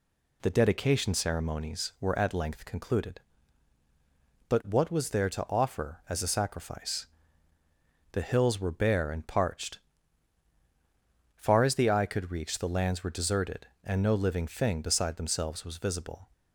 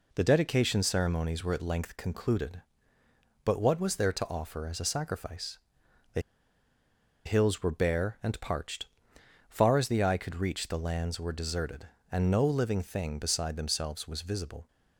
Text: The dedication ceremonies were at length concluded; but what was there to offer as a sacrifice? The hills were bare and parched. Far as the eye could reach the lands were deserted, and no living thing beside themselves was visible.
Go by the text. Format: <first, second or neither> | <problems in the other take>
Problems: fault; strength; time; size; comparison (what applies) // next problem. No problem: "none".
first | pauses between "The" and "hills"; at 6.1 s; 1.0 s long